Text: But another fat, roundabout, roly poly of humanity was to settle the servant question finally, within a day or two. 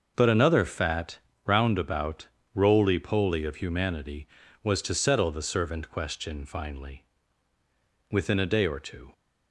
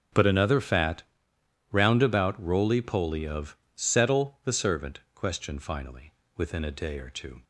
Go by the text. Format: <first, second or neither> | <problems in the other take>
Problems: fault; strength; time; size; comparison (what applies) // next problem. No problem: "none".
first | starts louder than the rest; strong; until 1.8 s; 8.5 dB; noticeable in the first // skips "humanity was to"; at 3.6 s // pauses between "servant" and "question"; slight; at 4.9 s; 0.16 s long